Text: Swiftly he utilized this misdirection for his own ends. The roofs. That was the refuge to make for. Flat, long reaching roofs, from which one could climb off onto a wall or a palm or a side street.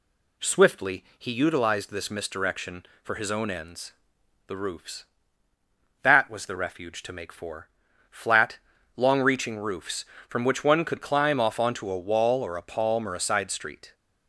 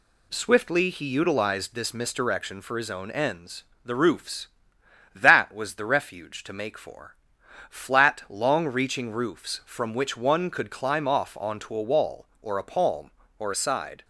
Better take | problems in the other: first | stops before "street"; at 14.0 s

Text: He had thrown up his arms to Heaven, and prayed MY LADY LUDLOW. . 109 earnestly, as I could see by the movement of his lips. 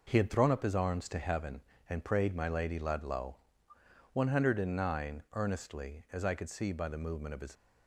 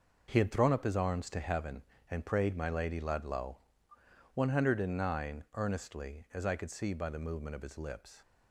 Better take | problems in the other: second | stops before "lips"; at 7.5 s

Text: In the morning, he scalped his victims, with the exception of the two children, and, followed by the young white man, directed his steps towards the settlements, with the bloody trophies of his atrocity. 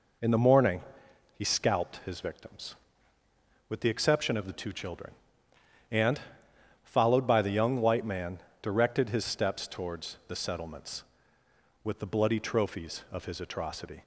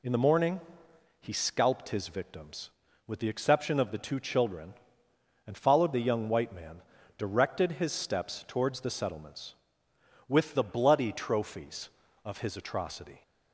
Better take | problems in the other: first | skips "by"; at 5.9 s

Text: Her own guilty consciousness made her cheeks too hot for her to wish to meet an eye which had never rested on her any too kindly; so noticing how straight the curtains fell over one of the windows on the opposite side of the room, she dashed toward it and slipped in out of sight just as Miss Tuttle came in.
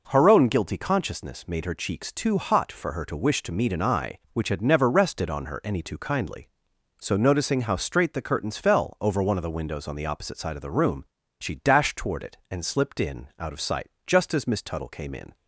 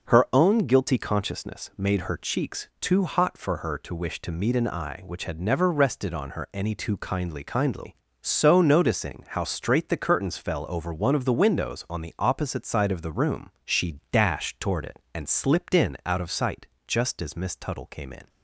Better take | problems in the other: first | says "kindly" twice; at 7.4 s // pauses between "sight" and "just"; slight; at 16.6 s; 0.20 s long; slight in the first

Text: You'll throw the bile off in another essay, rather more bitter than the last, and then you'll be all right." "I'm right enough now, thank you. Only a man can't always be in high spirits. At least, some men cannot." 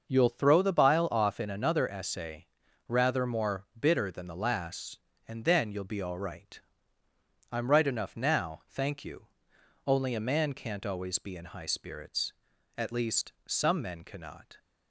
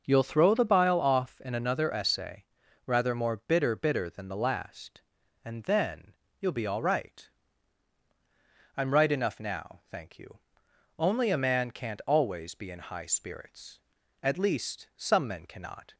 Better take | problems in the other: first | starts louder than the rest; noticeable; until 1.0 s; 6 dB; also in the first // says "bitter" twice; at 3.7 s // pauses between "then" and "you'll"; slight; at 6.1 s; 0.28 s long

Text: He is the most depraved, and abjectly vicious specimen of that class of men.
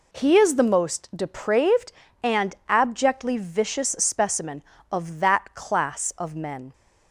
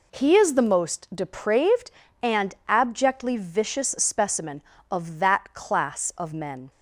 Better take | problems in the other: neither | none

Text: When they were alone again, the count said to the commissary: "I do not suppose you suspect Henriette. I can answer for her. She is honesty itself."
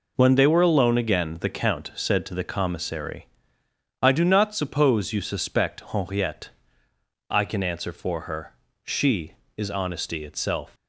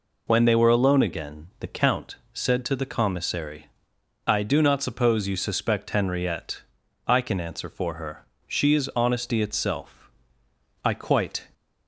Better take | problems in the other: first | pauses between "count" and "said"; slight; at 2.1 s; 0.18 s long // goes on to say "I quite"; noticeable; from 10.8 s on; 0.64 s long

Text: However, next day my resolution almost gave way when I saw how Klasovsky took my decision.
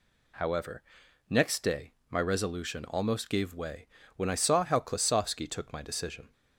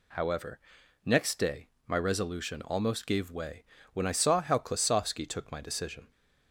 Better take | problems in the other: neither | pauses between "day" and "my"; slight; the same in both // pauses between "way" and "when"; slight; the same in both

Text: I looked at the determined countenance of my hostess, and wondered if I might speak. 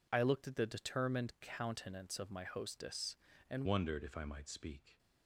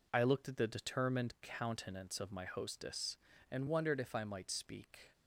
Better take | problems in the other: second | changes voice at "wondered"; from 3.6 s on; 1.3 s long

